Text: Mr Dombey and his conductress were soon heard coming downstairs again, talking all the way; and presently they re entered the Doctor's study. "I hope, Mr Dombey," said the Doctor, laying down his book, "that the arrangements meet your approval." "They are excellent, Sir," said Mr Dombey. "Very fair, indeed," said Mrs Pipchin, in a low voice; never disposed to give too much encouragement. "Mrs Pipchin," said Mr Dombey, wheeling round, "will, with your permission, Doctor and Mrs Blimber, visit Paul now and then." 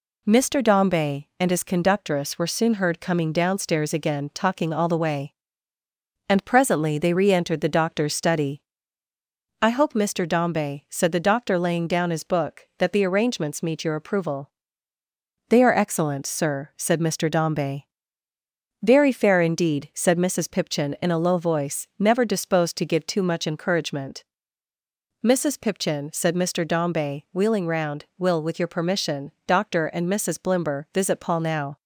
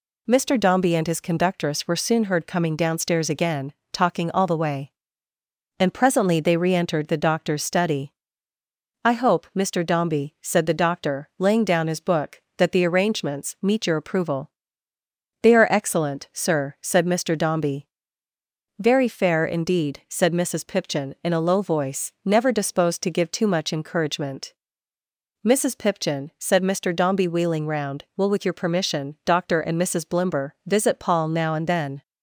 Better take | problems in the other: second | stops before "and then"; at 31.7 s

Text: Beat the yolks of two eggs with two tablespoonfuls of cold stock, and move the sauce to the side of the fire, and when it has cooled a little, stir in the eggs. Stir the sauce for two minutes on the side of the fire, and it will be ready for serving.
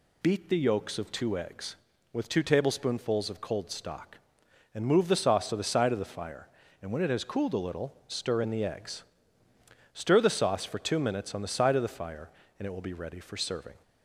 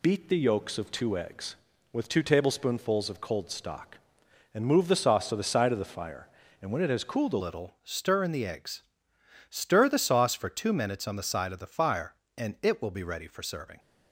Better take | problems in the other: first | changes voice at "little"; from 7.4 s on; 6.3 s long

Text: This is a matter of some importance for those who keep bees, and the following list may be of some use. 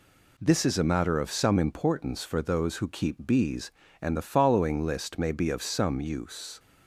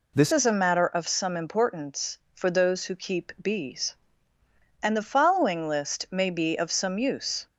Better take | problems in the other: first | changes voice at "is"; from 0.3 s on; 7.1 s long

